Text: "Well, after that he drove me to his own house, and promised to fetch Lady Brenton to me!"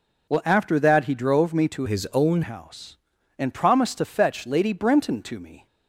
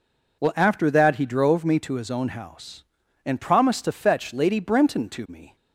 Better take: second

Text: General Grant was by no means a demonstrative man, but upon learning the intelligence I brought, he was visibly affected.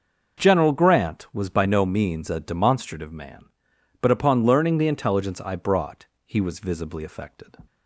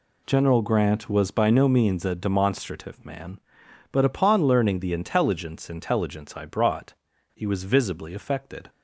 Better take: first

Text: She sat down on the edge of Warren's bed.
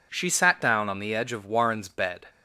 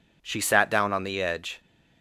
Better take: first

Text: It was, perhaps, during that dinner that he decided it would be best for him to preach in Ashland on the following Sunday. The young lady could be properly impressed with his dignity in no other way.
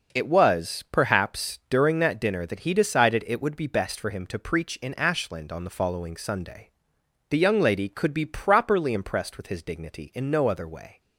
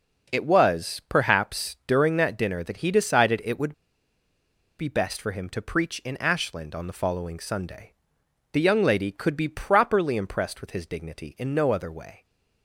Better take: first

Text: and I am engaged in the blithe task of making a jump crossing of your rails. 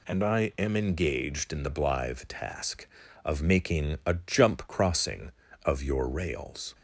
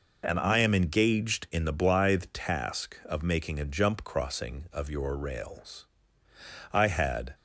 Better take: first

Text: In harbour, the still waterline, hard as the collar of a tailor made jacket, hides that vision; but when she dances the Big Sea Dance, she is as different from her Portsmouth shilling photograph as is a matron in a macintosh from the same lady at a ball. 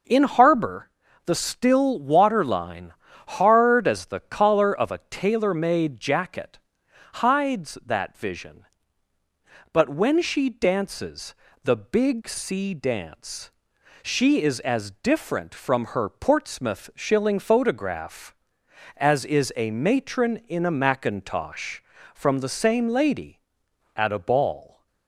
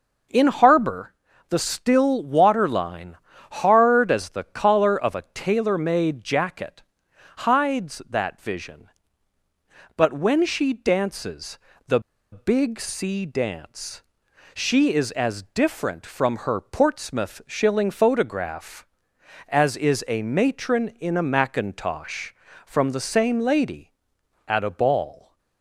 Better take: first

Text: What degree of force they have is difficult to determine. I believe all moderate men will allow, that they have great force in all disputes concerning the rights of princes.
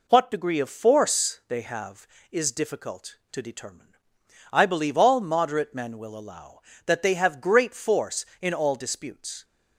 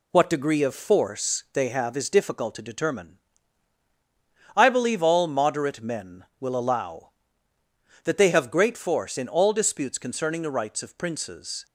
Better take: second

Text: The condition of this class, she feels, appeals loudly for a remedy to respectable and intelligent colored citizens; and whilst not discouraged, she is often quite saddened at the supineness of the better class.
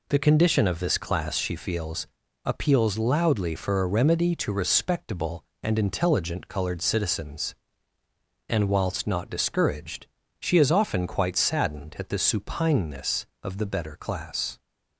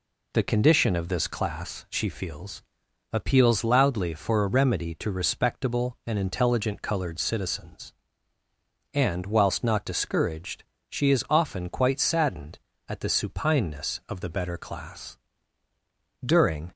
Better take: first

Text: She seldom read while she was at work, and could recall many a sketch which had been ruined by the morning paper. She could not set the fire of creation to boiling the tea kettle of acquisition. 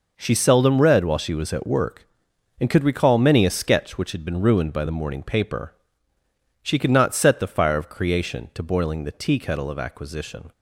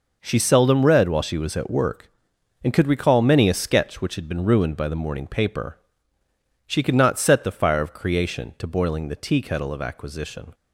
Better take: neither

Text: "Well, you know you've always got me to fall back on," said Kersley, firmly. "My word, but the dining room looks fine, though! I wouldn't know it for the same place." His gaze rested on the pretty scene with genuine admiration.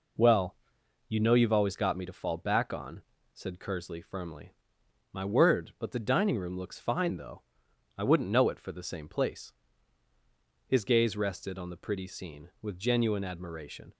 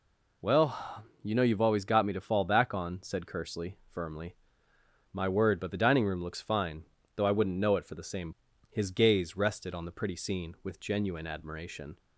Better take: first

